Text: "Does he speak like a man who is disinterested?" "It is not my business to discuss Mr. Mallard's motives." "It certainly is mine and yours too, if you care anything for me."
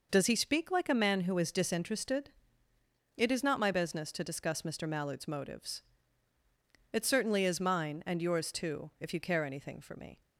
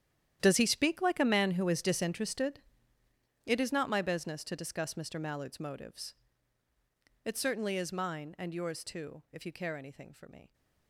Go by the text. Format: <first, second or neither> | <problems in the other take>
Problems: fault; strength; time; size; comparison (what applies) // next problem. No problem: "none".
first | gets quieter; strong; throughout; 16.5 dB